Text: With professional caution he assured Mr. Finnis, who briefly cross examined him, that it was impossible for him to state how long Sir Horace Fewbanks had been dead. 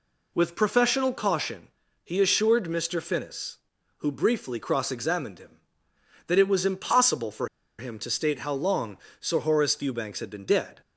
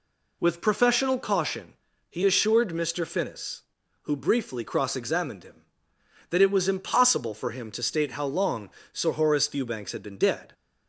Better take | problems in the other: second | pauses between "caution" and "he"; slight; at 1.6 s; 0.34 s long; slight in the second // pauses between "for" and "him"; slight; at 7.4 s; 0.32 s long // pauses between "long" and "Sir"; slight; at 8.9 s; 0.24 s long; slight in the second

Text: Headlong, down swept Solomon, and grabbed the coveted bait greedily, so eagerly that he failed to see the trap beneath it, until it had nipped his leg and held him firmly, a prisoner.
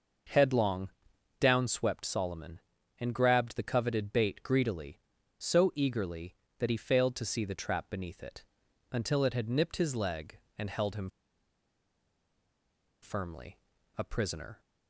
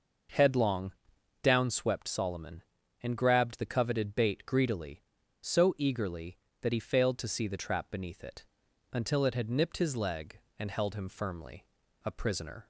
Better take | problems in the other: second | starts louder than the rest; noticeable; until 1.8 s; 6 dB; noticeable in the second // pauses between "him" and "firmly"; strong; at 11.0 s; 1.9 s long

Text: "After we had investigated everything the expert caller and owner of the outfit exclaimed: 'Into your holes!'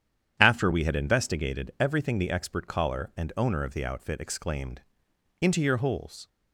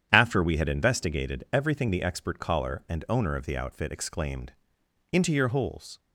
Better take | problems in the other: neither | starts louder than the rest; strong; the same in both

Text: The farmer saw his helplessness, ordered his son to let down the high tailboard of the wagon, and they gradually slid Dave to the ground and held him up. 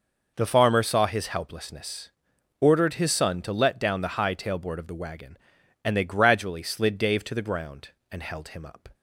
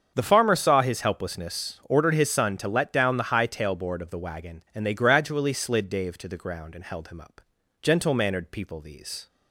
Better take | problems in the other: first | starts louder than the rest; strong; until 1.1 s; 7 dB // goes on to say "Gentle mannered people these"; from 7.8 s on; 1.4 s long

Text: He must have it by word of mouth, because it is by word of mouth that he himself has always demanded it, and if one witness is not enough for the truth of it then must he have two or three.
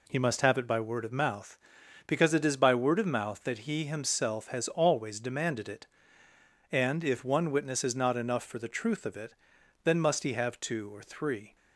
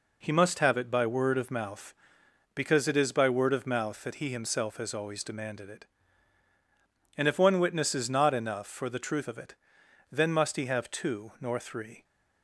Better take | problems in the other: first | pauses between "it" and "then"; noticeable; at 9.5 s; 0.56 s long; noticeable in the first // says "nor" for "or"; at 11.3 s

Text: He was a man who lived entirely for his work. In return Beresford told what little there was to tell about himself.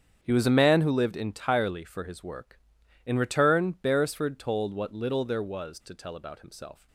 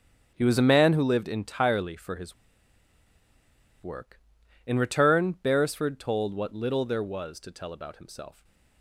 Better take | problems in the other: first | starts louder than the rest; strong; until 1.3 s; 8 dB; strong in the first // pauses between "his" and "work"; strong; at 2.3 s; 1.4 s long

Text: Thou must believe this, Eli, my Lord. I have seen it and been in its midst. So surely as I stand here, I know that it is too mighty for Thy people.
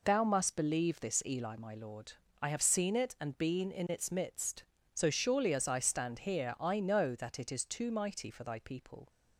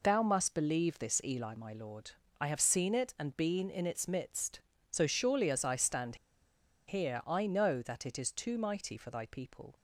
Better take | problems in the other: first | pauses between "stand" and "here"; noticeable; at 6.1 s; 0.72 s long

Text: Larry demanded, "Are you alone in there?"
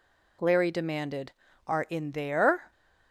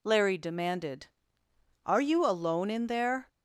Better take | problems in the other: second | skips "you alone"; at 1.8 s

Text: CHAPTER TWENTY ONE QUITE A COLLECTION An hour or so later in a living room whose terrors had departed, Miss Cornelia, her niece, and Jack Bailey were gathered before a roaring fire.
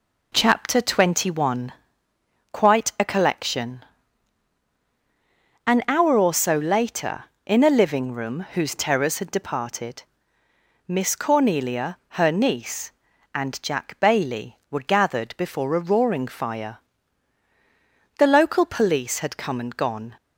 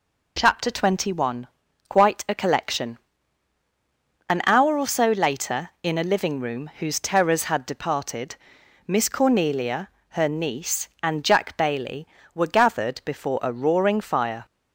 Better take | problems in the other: second | pauses between "ONE" and "QUITE"; noticeable; at 1.7 s; 0.80 s long; also in the second // pauses between "COLLECTION" and "An"; strong; at 3.8 s; 1.8 s long; strong in the second // goes on to say "The local police had come and gone"; strong; from 18.1 s on; 1.9 s long

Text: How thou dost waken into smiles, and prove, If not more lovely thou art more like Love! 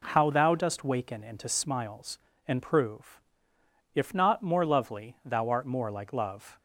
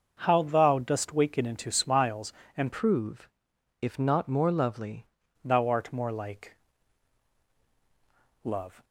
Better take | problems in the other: first | starts louder than the rest; noticeable; until 1.2 s; 6 dB // changes voice from "prove" to "lovely"; from 2.7 to 5.0 s; 2.3 s long // pauses between "like" and "Love"; strong; at 6.5 s; 1.9 s long

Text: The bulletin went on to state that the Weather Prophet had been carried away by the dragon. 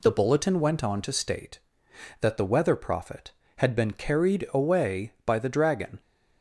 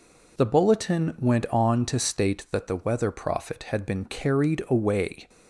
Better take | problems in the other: first | stops before "by the dragon"; at 5.2 s

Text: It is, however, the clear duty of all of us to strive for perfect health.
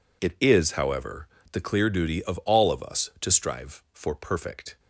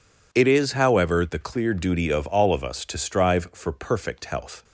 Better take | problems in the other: second | stops before "health"; at 4.7 s

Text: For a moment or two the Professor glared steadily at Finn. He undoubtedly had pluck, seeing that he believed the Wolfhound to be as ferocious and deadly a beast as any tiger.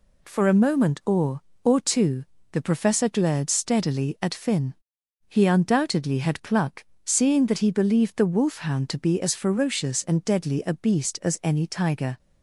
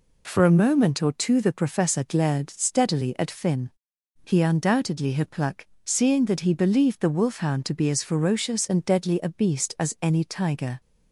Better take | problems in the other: second | says "or" twice; at 1.6 s // pauses between "two" and "the"; slight; at 2.2 s; 0.28 s long

